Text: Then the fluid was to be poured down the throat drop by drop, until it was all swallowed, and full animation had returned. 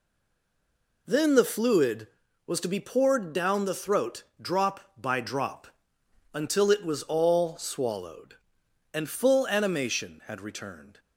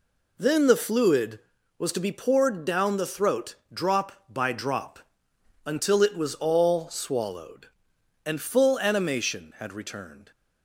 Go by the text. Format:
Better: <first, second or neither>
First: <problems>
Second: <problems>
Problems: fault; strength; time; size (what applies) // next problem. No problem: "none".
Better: second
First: stays silent before the first word; until 1.0 s; 1.0 s long // pauses between "throat" and "drop"; slight; at 4.2 s; 0.18 s long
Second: pauses between "throat" and "drop"; slight; at 3.5 s; 0.18 s long